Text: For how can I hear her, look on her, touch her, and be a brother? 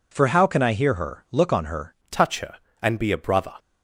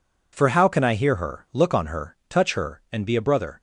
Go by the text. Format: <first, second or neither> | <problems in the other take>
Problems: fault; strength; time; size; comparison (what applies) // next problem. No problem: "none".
second | changes voice at "touch"; from 2.0 s on; 1.5 s long